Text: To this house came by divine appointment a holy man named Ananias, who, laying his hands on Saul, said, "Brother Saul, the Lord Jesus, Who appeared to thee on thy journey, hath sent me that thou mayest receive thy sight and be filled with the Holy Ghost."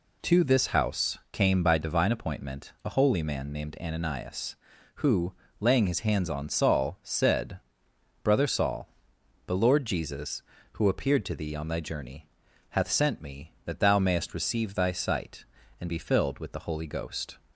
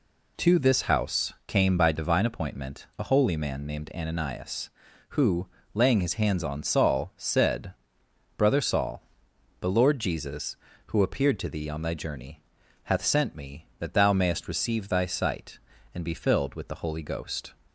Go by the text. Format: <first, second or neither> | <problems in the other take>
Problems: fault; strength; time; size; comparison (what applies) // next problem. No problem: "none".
neither | none